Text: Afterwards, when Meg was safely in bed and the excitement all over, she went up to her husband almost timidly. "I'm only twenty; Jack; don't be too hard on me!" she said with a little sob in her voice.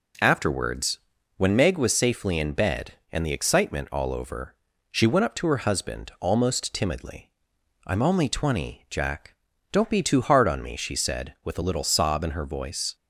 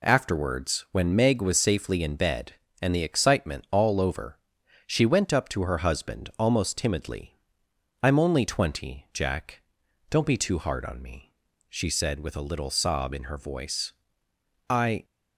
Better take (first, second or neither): first